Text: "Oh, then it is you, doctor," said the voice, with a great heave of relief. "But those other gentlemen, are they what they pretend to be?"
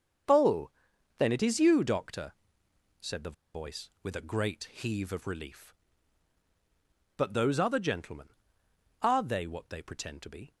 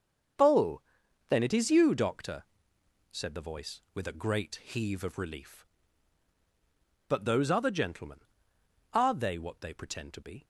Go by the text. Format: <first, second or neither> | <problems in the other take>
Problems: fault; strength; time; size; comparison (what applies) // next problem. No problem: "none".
second | starts louder than the rest; until 1.7 s; 7 dB; also in the second // pauses between "the" and "voice"; slight; at 3.3 s; 0.21 s long